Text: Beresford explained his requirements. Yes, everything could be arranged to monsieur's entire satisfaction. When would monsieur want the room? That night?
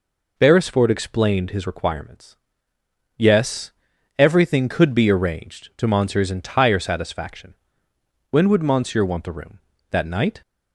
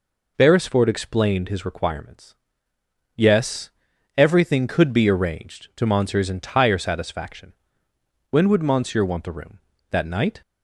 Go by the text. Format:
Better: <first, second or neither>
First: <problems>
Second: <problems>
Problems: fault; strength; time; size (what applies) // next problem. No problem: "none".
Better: neither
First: none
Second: none